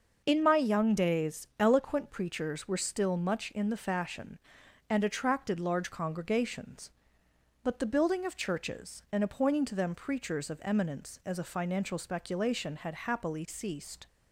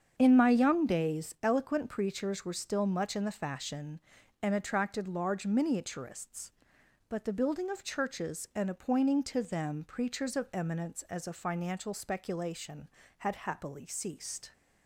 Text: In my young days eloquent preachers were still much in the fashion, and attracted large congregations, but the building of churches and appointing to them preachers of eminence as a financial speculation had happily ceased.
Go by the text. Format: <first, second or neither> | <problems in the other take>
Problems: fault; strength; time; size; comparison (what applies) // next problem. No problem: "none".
first | starts louder than the rest; strong; until 1.1 s; 7.5 dB; noticeable in the first // says "miniaturists" for "congregations"; at 5.4 s